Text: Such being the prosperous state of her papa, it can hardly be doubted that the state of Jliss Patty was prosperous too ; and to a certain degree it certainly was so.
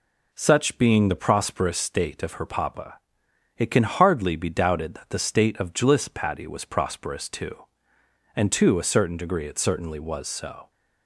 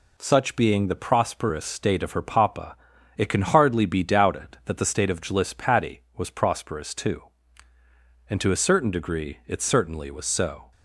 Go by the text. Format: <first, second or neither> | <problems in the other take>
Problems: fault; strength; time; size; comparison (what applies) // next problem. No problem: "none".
neither | none